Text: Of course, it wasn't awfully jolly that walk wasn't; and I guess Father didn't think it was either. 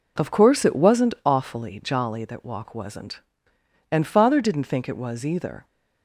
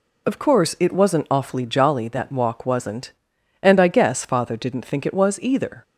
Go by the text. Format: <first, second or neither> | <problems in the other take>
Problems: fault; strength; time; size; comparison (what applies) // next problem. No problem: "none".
second | skips "I guess"; at 4.0 s